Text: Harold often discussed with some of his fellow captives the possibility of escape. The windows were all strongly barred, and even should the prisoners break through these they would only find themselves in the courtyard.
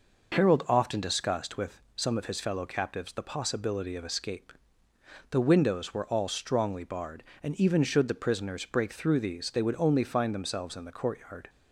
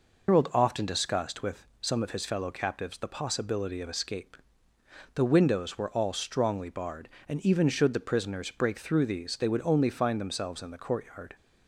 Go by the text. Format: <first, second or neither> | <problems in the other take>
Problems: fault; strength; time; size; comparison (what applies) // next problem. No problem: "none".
first | loses the start of "Harold"; at 0.2 s; 110 ms